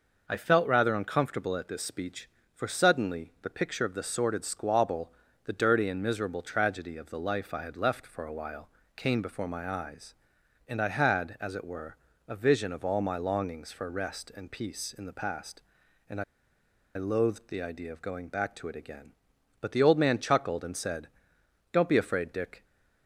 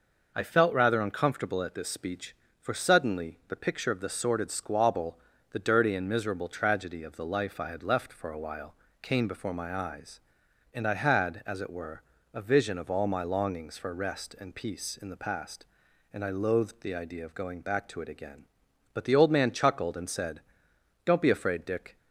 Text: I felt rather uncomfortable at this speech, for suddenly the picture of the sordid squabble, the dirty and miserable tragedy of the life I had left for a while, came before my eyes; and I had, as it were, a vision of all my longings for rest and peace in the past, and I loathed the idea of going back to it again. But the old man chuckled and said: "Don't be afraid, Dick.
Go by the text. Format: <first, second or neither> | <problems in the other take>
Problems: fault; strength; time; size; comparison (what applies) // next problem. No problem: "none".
second | pauses between "I" and "loathed"; noticeable; at 16.2 s; 0.71 s long